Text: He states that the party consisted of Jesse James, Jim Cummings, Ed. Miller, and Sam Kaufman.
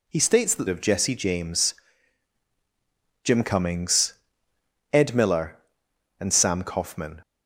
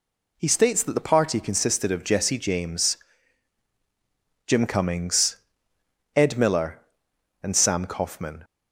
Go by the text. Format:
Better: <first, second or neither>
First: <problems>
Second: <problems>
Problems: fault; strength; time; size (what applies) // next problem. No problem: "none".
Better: second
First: skips "the party consisted"; at 0.6 s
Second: none